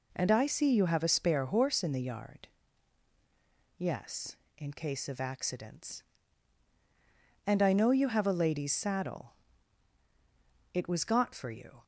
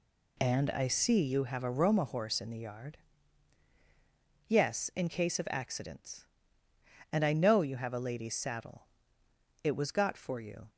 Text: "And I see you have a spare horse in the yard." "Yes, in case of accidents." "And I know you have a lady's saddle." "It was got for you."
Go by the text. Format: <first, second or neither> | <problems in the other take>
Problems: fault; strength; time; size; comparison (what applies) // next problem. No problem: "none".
first | says "roma" for "spare"; at 1.7 s